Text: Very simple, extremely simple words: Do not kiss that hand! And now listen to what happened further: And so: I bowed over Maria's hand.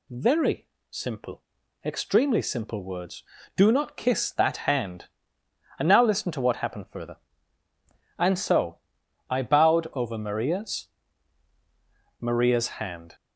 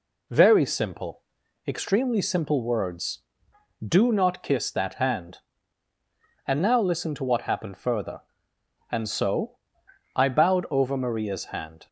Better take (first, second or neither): second